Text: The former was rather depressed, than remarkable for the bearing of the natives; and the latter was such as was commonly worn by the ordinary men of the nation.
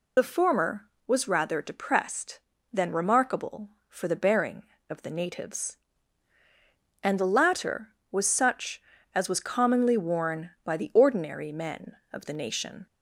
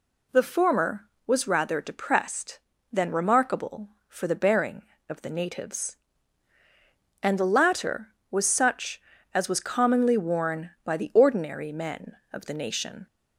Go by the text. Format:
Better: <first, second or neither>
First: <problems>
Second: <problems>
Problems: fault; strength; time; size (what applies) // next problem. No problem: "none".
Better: second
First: loses the start of "The"; at 0.1 s; 55 ms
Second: none